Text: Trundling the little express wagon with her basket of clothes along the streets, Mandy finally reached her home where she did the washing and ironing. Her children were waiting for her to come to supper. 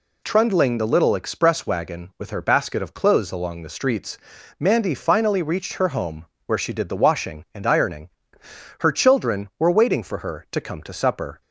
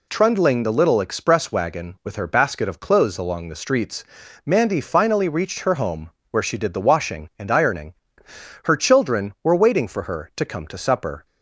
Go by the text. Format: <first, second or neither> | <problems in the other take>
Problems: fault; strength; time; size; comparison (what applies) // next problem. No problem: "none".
neither | pauses between "home" and "where"; slight; the same in both